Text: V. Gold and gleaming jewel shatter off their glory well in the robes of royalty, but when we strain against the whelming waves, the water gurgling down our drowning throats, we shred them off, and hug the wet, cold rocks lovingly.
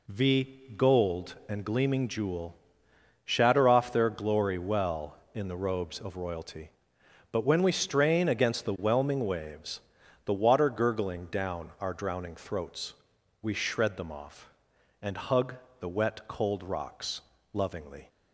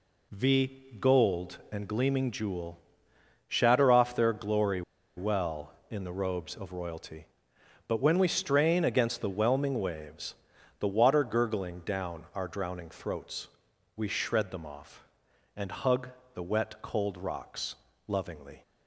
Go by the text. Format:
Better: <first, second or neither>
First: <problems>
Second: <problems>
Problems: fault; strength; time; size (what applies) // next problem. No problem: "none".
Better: first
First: pauses between "jewel" and "shatter"; noticeable; at 2.5 s; 0.68 s long // pauses between "hug" and "the"; slight; at 15.5 s; 0.24 s long // pauses between "rocks" and "lovingly"; slight; at 17.1 s; 0.32 s long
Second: pauses between "jewel" and "shatter"; noticeable; at 2.7 s; 0.68 s long // pauses between "glory" and "well"; slight; at 4.8 s; 0.35 s long // pauses between "hug" and "the"; slight; at 16.0 s; 0.24 s long // pauses between "rocks" and "lovingly"; slight; at 17.7 s; 0.32 s long